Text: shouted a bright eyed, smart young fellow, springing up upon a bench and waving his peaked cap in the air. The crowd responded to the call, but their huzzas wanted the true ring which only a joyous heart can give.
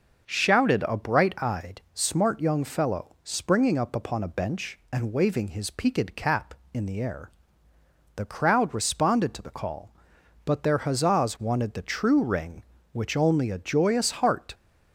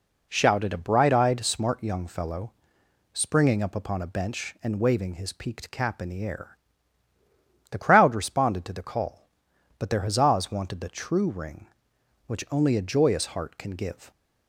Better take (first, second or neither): second